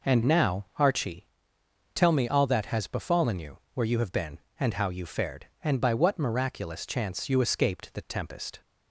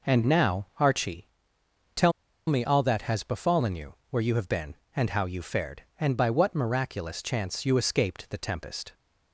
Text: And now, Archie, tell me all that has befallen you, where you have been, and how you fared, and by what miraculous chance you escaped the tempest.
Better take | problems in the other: first | pauses between "tell" and "me"; slight; at 2.1 s; 0.35 s long

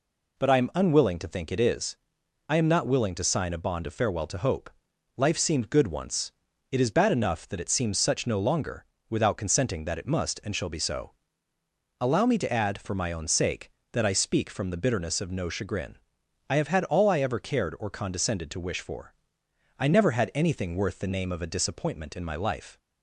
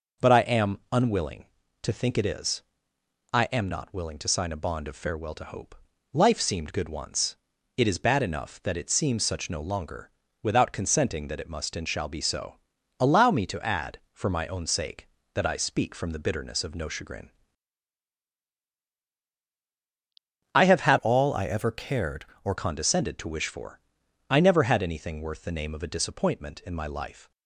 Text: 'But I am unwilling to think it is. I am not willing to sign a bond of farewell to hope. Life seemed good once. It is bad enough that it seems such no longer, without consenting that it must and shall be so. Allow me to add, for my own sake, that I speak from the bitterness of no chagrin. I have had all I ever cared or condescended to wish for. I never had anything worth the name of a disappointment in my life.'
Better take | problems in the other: first | changes voice from "all" to "or"; from 20.9 to 22.5 s; 1.6 s long

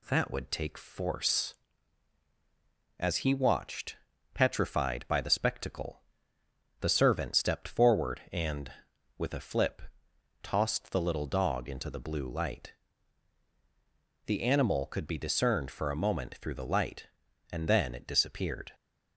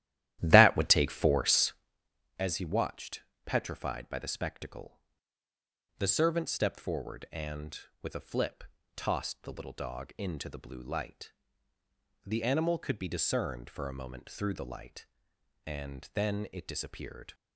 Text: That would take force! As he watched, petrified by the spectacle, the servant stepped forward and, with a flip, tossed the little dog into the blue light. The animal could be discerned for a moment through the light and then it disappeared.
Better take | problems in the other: first | starts louder than the rest; strong; until 1.9 s; 13.5 dB

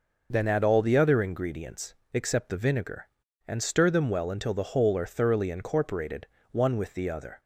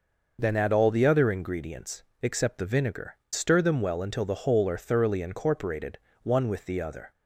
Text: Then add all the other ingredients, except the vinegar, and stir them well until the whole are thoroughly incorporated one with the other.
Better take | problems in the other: first | skips "and"; at 3.2 s // pauses between "incorporated" and "one"; slight; at 5.9 s; 0.24 s long; slight in the first

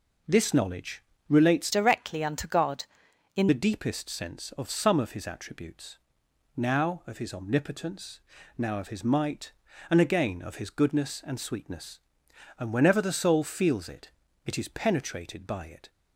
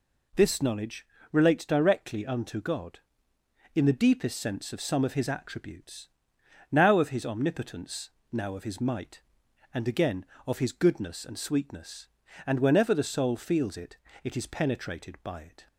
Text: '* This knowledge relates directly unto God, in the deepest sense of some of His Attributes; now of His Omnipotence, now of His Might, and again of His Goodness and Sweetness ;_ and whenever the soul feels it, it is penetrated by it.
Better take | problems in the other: second | pauses between "knowledge" and "relates"; slight; at 1.0 s; 0.26 s long; slight in the second // changes voice from "directly" to "in"; from 1.7 to 3.4 s; 1.7 s long

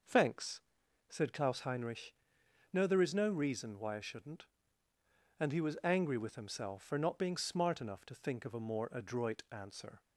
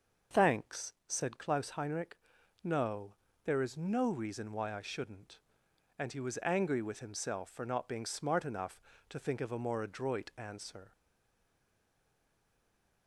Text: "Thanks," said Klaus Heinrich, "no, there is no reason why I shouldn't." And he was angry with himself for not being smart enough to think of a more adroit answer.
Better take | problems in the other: first | starts louder than the rest; noticeable; until 1.4 s; 6 dB // stays silent after the last word; from 10.9 s on; 2.1 s long

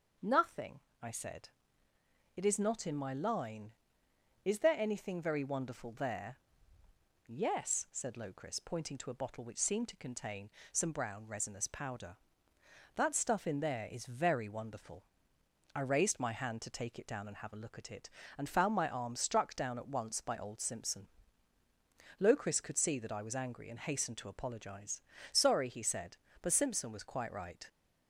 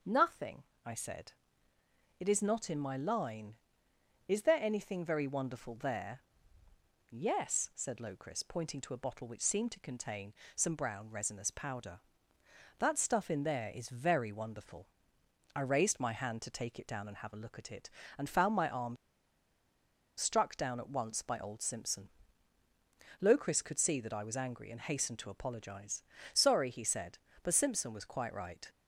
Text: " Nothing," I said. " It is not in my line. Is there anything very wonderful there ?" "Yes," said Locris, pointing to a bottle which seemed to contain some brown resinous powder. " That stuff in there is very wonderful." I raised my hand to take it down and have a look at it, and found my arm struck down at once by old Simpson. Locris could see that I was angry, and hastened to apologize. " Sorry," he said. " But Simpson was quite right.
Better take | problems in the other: first | pauses between "contain" and "some"; slight; at 10.3 s; 0.22 s long; slight in the first // pauses between "arm" and "struck"; at 18.9 s; 1.2 s long

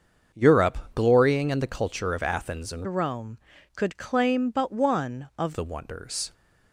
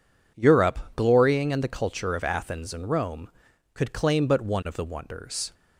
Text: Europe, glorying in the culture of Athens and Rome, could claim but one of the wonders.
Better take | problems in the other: second | starts louder than the rest; until 1.5 s; 7 dB // changes voice from "Rome" to "of"; from 2.8 to 5.5 s; 2.7 s long

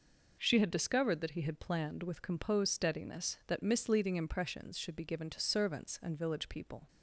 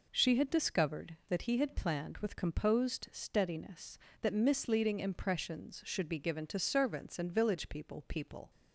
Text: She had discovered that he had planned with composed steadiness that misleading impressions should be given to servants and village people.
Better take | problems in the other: first | says "people" twice; at 8.0 s

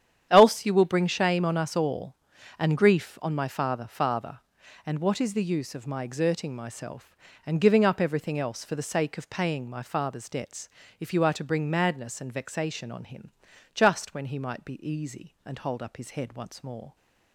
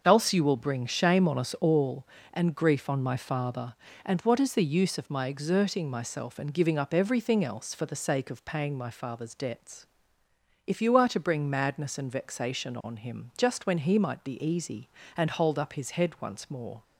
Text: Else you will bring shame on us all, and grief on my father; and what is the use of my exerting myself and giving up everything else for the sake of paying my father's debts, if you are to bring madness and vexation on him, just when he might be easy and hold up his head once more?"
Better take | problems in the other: second | starts louder than the rest; strong; until 1.3 s; 9.5 dB; also in the second // says "father" twice; at 3.8 s

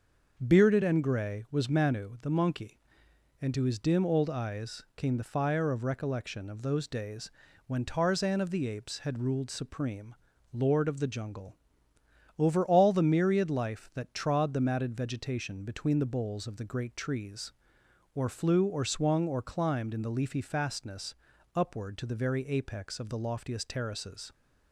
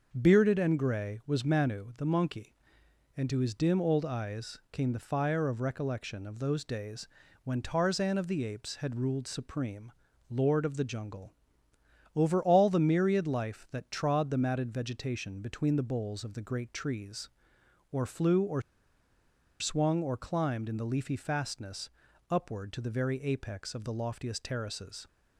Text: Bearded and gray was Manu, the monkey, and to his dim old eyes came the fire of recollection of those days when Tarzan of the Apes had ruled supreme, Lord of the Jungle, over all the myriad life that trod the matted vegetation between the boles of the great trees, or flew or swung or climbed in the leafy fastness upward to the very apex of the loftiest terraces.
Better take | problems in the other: first | starts louder than the rest; until 1.1 s; 6.5 dB; also in the first // pauses between "days" and "when"; slight; at 7.0 s; 0.36 s long; slight in the first // pauses between "or" and "swung"; at 18.6 s; 0.98 s long // pauses between "fastness" and "upward"; at 21.8 s; 0.40 s long; also in the first

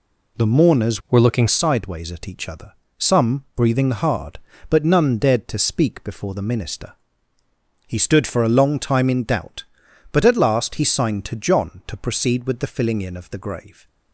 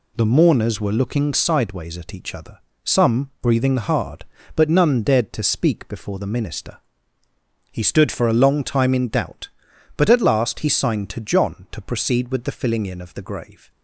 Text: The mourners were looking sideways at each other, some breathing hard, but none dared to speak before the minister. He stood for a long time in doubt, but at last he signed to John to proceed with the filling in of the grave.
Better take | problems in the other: second | changes voice from "were" to "looking"; from 1.1 to 1.4 s; 0.3 s long

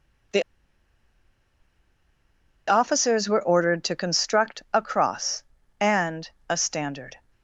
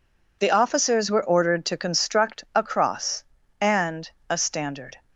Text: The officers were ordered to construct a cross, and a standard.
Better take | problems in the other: second | pauses between "The" and "officers"; strong; at 0.4 s; 2.2 s long // pauses between "and" and "a"; slight; at 6.2 s; 0.22 s long; slight in the second

